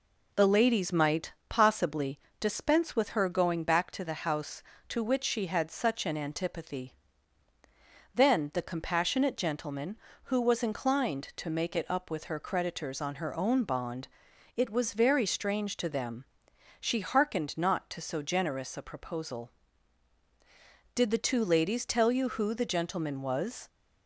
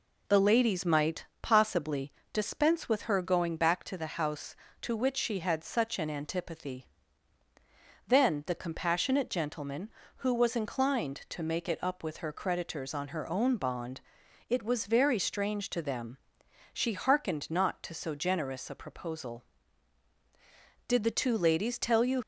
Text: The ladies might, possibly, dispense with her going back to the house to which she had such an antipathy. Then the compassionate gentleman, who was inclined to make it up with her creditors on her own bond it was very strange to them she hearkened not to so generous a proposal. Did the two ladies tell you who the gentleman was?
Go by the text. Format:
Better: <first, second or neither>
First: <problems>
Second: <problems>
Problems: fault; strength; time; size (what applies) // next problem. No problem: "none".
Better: first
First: pauses between "bond" and "it"; noticeable; at 14.0 s; 0.46 s long // pauses between "them" and "she"; noticeable; at 16.2 s; 0.54 s long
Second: pauses between "bond" and "it"; noticeable; at 14.0 s; 0.46 s long // pauses between "them" and "she"; noticeable; at 16.1 s; 0.54 s long // stops before "who the gentleman was"; at 22.2 s